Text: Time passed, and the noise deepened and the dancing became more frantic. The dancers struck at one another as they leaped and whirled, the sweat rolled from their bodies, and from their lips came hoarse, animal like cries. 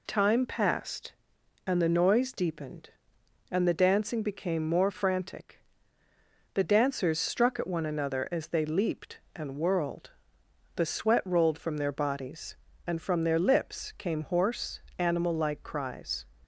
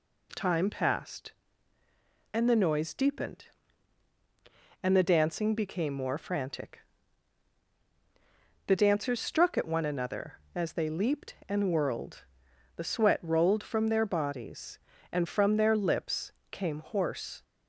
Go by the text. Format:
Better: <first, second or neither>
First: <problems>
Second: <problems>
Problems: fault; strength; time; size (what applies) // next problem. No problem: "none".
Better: first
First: none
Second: pauses between "lips" and "came"; slight; at 16.3 s; 0.20 s long // stops before "animal like cries"; at 17.4 s